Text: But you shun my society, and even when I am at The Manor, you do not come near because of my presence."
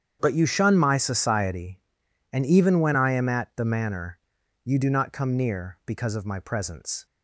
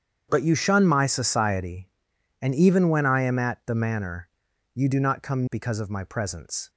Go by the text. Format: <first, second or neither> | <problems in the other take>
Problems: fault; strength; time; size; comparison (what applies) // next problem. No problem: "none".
first | starts louder than the rest; strong; until 1.3 s; 8 dB; strong in the first // skips "near"; at 5.4 s